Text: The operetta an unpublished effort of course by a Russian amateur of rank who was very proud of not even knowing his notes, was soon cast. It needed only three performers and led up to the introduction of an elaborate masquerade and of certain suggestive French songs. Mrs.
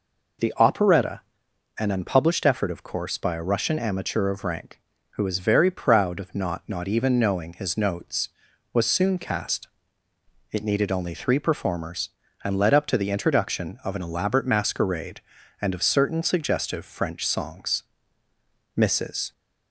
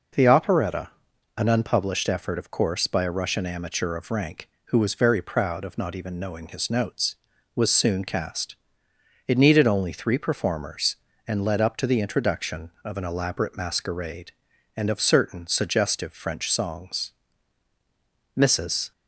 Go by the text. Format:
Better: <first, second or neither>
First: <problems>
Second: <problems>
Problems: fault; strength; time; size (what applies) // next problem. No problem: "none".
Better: second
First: pauses between "operetta" and "an"; noticeable; at 1.1 s; 0.58 s long // says "not" twice; at 6.6 s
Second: pauses between "operetta" and "an"; noticeable; at 0.8 s; 0.46 s long